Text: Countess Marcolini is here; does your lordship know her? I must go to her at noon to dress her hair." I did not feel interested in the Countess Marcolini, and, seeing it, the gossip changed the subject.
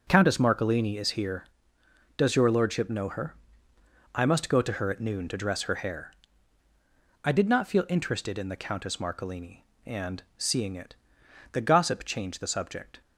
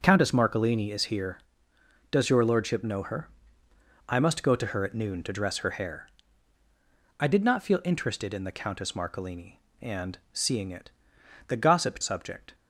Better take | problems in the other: first | starts louder than the rest; until 1.0 s; 7 dB; also in the first // skips "changed the"; at 12.0 s

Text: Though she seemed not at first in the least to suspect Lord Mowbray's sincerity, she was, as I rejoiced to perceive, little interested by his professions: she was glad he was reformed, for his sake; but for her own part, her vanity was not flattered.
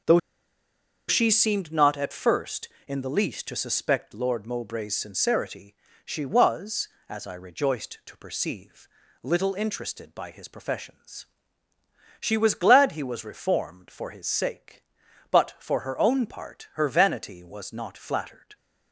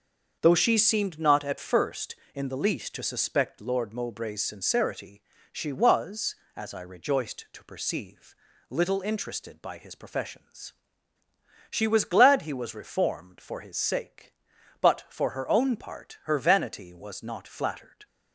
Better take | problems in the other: second | starts louder than the rest; until 1.9 s; 6.5 dB; also in the second // pauses between "Though" and "she"; noticeable; at 0.1 s; 0.89 s long

